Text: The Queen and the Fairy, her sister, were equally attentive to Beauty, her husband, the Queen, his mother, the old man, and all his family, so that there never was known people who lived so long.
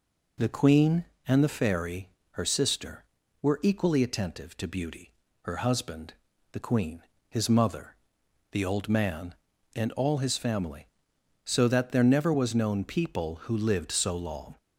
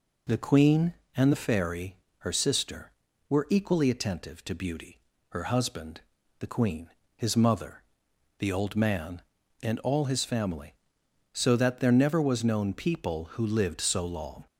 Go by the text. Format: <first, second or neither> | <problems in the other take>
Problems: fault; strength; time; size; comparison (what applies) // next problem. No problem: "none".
neither | none